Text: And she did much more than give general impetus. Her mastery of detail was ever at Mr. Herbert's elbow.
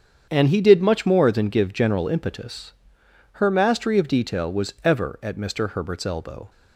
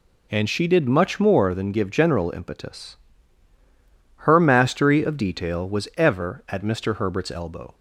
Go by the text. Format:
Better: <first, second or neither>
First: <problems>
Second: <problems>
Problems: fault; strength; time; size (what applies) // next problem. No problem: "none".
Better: second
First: starts louder than the rest; strong; until 1.3 s; 7.5 dB // says "he" for "she"; at 0.4 s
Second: none